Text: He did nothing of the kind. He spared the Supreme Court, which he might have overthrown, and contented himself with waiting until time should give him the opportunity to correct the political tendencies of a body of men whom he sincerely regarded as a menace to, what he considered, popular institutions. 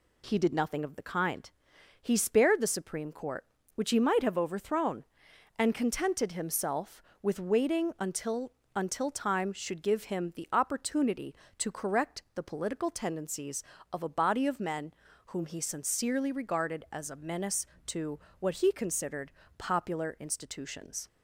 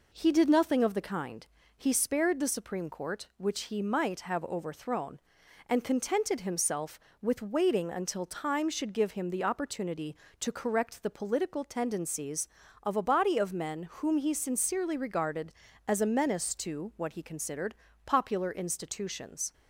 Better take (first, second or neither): second